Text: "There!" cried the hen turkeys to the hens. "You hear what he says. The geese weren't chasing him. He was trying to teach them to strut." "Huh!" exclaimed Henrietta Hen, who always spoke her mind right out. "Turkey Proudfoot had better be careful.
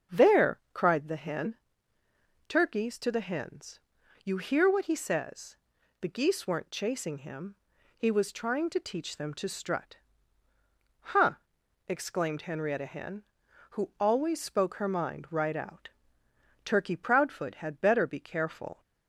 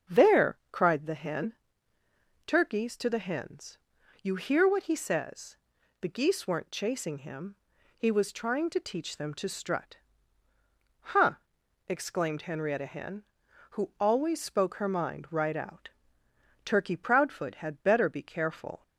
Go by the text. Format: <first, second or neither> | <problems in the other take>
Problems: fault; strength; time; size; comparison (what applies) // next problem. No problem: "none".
neither | starts louder than the rest; the same in both // pauses between "hen" and "turkeys"; noticeable; the same in both